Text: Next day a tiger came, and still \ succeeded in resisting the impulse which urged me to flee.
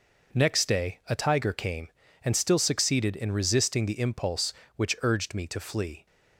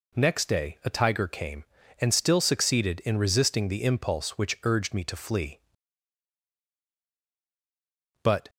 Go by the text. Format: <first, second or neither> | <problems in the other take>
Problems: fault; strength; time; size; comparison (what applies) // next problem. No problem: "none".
first | goes on to say "But"; slight; from 8.2 s on; 0.26 s long